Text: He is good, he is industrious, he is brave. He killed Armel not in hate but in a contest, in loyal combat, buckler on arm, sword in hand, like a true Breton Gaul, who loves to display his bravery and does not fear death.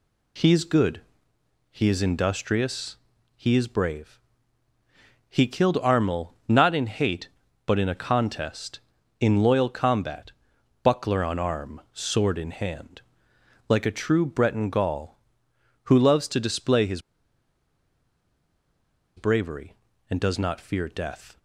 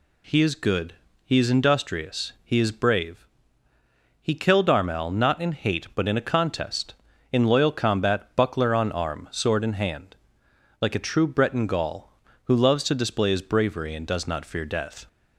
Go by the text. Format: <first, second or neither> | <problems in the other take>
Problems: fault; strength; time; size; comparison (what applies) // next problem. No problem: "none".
second | pauses between "his" and "bravery"; strong; at 17.0 s; 2.1 s long